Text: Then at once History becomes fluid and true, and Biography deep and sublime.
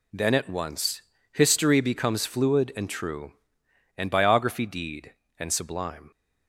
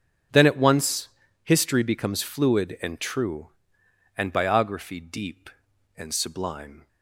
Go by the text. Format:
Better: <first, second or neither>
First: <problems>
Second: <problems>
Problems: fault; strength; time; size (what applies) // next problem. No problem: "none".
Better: second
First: pauses between "once" and "History"; slight; at 1.0 s; 0.30 s long // says "deed" for "deep"; at 4.6 s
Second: pauses between "once" and "History"; slight; at 1.0 s; 0.36 s long